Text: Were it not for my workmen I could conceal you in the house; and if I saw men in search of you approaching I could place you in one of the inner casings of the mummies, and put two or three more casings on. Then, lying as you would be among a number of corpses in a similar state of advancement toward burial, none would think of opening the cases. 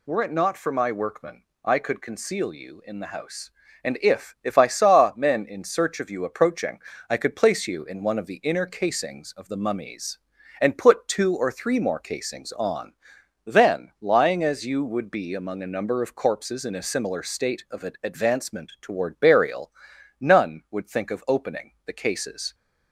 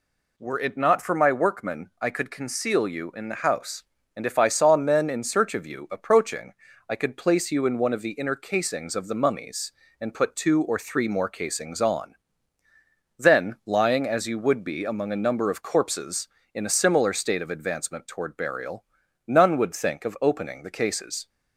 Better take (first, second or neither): second